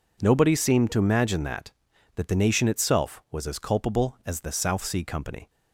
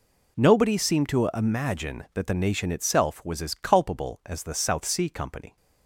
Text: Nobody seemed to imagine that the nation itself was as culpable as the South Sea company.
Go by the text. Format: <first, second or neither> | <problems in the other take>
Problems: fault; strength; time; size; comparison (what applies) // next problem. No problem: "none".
second | says "that" twice; at 2.1 s